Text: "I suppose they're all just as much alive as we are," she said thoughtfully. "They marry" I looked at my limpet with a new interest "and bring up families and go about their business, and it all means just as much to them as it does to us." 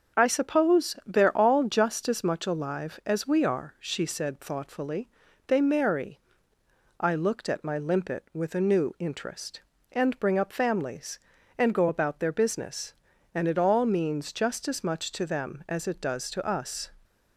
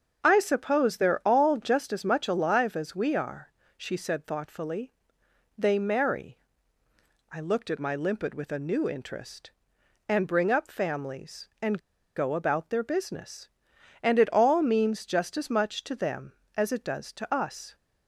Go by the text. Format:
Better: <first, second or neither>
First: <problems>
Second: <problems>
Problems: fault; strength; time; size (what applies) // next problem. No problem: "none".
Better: first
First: starts louder than the rest; until 1.2 s; 7 dB // pauses between "marry" and "I"; noticeable; at 6.1 s; 0.80 s long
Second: starts louder than the rest; until 1.2 s; 7 dB // pauses between "marry" and "I"; noticeable; at 6.4 s; 0.90 s long // pauses between "and" and "go"; at 11.7 s; 0.36 s long